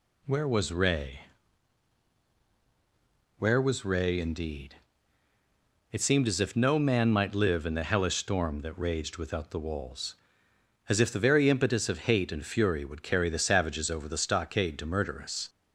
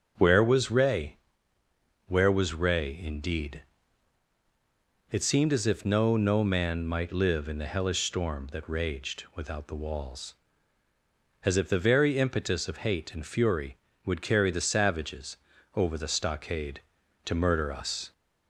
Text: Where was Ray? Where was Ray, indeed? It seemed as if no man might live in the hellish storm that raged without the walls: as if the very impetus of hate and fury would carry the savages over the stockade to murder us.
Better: first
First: none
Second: starts louder than the rest; until 1.1 s; 7 dB // says "no" twice; at 6.1 s // pauses between "savages" and "over"; at 15.3 s; 0.38 s long

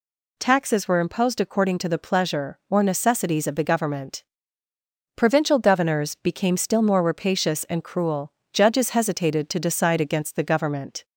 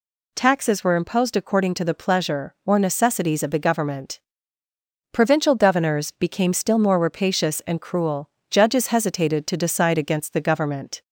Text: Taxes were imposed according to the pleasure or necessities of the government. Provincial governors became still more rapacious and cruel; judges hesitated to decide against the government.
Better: neither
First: none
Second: none

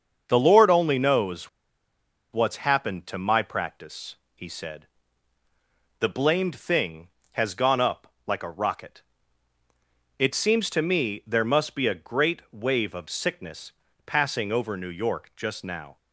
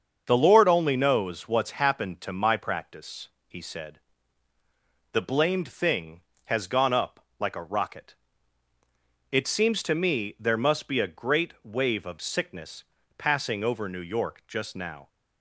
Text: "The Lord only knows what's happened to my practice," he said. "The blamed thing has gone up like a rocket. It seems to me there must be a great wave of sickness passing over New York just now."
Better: second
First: starts louder than the rest; until 1.2 s; 7 dB // pauses between "knows" and "what's"; noticeable; at 1.4 s; 0.83 s long // pauses between "sickness" and "passing"; slight; at 13.7 s; 0.32 s long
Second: starts louder than the rest; until 1.2 s; 7 dB // pauses between "sickness" and "passing"; slight; at 12.8 s; 0.32 s long

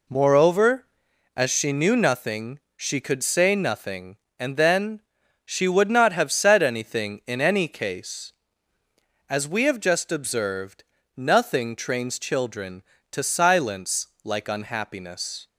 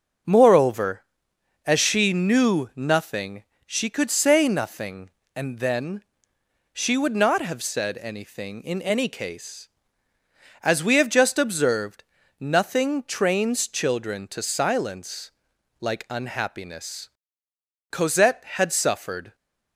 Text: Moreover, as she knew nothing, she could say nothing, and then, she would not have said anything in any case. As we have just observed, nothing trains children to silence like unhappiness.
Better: first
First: pauses between "silence" and "like"; slight; at 14.0 s; 0.16 s long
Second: starts louder than the rest; until 1.9 s; 6.5 dB // pauses between "silence" and "like"; noticeable; at 15.3 s; 0.48 s long // goes on to say "Cosette had suffered"; from 17.9 s on; 1.4 s long

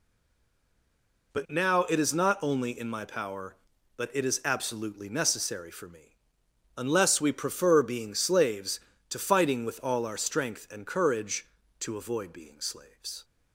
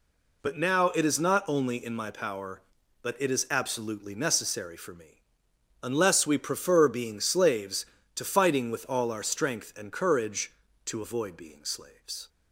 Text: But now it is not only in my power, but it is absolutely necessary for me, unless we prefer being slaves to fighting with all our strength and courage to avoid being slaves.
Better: second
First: stays silent before the first word; noticeable; until 1.3 s; 1.3 s long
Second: none

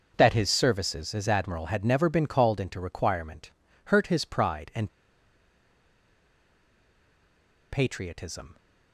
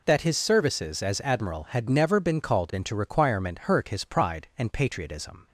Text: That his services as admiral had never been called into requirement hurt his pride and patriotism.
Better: second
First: starts louder than the rest; until 1.1 s; 6 dB // pauses between "requirement" and "hurt"; slight; at 3.5 s; 0.34 s long // pauses between "and" and "patriotism"; strong; at 4.8 s; 2.8 s long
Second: none

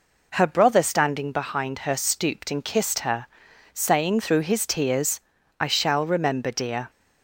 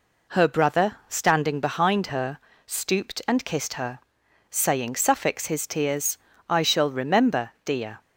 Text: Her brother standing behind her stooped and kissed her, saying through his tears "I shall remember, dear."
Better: first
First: pauses between "tears" and "I"; at 5.1 s; 0.40 s long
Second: pauses between "her" and "stooped"; slight; at 2.3 s; 0.28 s long // says "suffix" for "through"; at 4.9 s // pauses between "tears" and "I"; slight; at 6.1 s; 0.32 s long

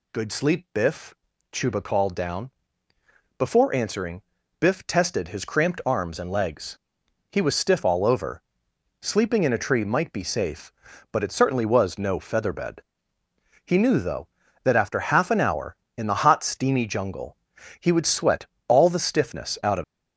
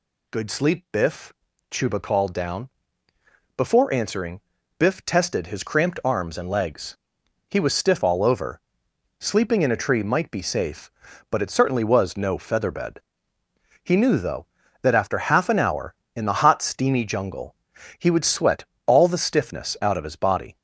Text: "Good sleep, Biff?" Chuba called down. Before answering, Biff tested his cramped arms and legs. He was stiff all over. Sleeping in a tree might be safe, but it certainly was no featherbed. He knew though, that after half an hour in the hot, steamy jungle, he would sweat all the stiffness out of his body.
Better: second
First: pauses between "sweat" and "all"; slight; at 18.4 s; 0.20 s long // stops before "his body"; at 19.8 s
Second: pauses between "sweat" and "all"; slight; at 18.6 s; 0.20 s long

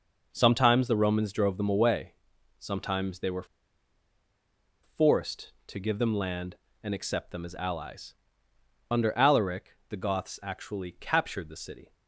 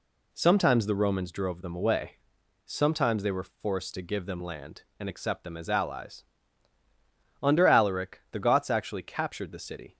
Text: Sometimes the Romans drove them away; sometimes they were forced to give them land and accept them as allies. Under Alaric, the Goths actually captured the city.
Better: second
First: pauses between "were" and "forced"; strong; at 3.4 s; 1.3 s long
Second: none

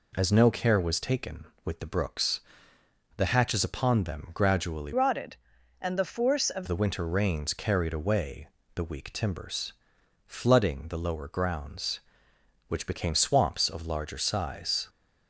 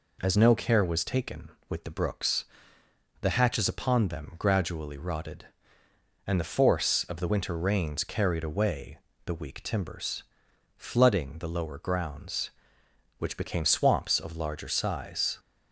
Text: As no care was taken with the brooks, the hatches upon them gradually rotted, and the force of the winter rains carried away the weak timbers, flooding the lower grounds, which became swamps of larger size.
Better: second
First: changes voice from "rotted" to "of"; from 4.9 to 6.6 s; 1.7 s long // pauses between "away" and "the"; slight; at 8.4 s; 0.30 s long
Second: pauses between "away" and "the"; slight; at 8.9 s; 0.30 s long

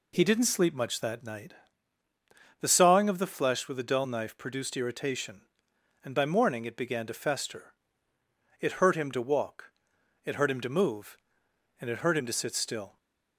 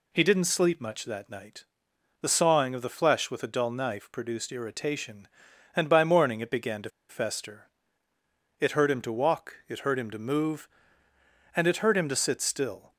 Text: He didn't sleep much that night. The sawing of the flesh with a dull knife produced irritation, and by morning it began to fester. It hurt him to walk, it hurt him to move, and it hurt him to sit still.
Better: first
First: none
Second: pauses between "to" and "fester"; slight; at 6.8 s; 0.19 s long

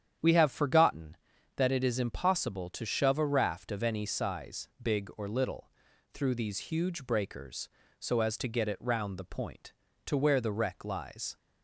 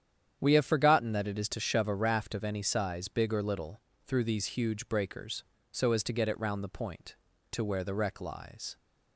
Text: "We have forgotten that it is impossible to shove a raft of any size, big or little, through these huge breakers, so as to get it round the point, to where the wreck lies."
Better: first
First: starts louder than the rest; strong; until 1.6 s; 9 dB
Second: starts louder than the rest; strong; until 1.4 s; 9 dB // skips "impossible"; at 1.4 s

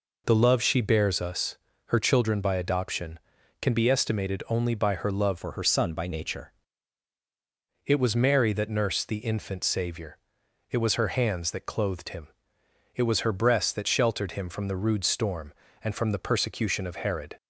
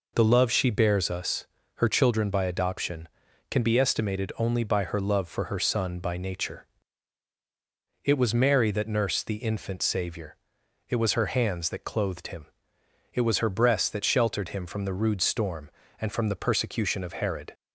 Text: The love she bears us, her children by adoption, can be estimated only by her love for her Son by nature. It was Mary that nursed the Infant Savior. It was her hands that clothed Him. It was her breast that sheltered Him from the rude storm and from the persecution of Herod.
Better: second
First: changes voice from "for" to "nature"; from 5.3 to 6.5 s; 1.2 s long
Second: none

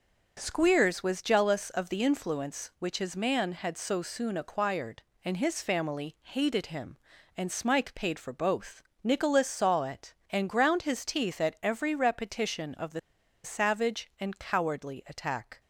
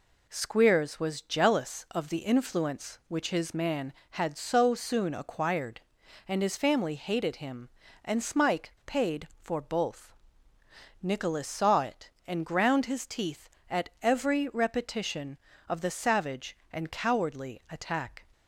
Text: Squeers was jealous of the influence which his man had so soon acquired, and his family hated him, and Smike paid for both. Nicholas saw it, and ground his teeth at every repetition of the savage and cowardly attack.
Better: second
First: pauses between "the" and "savage"; at 12.9 s; 0.44 s long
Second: none

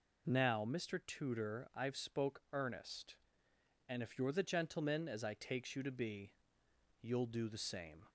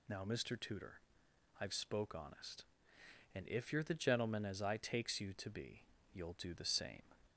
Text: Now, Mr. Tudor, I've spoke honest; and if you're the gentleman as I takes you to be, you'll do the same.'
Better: second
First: says "earnest" for "honest"; at 2.5 s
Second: none

